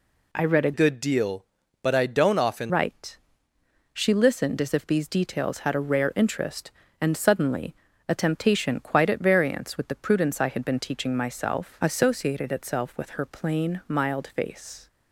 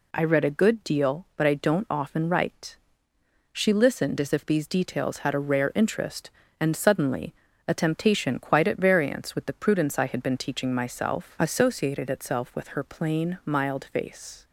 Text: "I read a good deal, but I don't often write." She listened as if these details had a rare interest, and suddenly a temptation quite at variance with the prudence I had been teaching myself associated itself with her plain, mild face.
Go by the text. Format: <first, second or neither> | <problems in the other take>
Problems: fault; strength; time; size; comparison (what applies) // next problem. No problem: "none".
second | changes voice from "good" to "often"; from 0.7 to 2.7 s; 2.0 s long // pauses between "suddenly" and "a"; slight; at 7.7 s; 0.32 s long; slight in the second